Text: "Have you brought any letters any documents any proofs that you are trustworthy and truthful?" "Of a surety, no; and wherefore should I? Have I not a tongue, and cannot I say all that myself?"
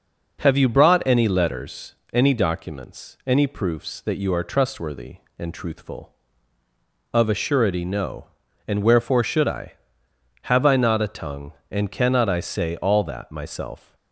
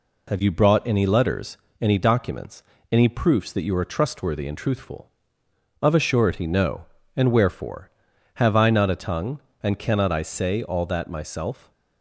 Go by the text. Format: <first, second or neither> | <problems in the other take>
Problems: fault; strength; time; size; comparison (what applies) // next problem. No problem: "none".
first | pauses between "letters" and "any"; slight; at 1.5 s; 0.24 s long; slight in the first // pauses between "documents" and "any"; slight; at 2.6 s; 0.30 s long // skips "should I"; at 8.1 s